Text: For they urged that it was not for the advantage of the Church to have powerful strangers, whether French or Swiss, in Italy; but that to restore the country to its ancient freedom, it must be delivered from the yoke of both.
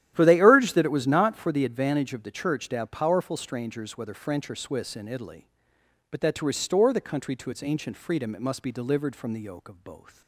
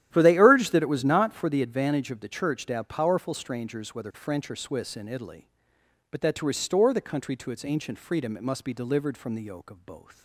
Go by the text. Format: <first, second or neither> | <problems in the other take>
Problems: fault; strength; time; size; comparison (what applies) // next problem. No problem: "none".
neither | starts louder than the rest; strong; the same in both